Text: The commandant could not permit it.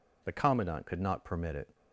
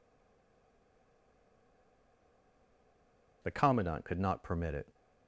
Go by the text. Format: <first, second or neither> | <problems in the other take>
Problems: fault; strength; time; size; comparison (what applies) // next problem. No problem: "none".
first | stays silent before the first word; strong; until 3.4 s; 3.4 s long